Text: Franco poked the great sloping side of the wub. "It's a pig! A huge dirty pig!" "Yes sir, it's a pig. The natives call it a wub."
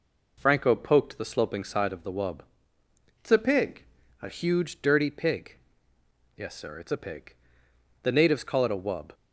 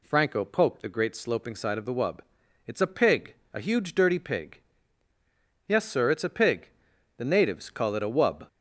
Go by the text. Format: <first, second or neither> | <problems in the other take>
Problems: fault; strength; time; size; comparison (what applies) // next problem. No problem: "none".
second | skips "great"; at 1.2 s